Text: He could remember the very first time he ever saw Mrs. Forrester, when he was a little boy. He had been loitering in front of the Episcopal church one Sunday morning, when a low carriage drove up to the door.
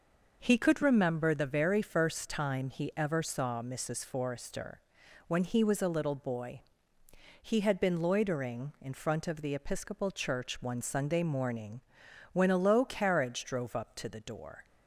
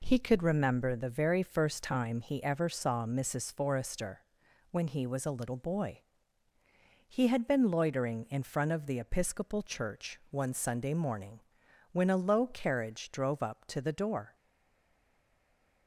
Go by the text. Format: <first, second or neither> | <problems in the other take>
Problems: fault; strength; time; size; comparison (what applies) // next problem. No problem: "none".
first | stays silent after the last word; noticeable; from 14.3 s on; 1.5 s long